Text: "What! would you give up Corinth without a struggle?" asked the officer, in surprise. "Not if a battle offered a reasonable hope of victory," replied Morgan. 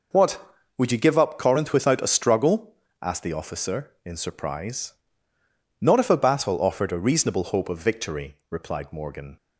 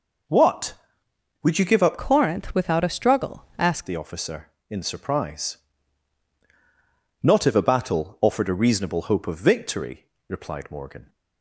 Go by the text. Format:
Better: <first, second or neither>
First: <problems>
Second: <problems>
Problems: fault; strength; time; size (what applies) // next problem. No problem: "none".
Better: first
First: none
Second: changes voice from "Corinth" to "asked"; from 1.9 to 3.8 s; 1.9 s long